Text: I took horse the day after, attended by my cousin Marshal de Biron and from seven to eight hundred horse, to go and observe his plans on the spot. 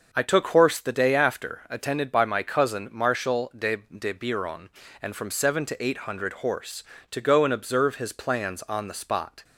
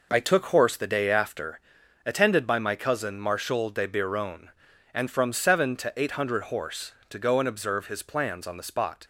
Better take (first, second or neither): second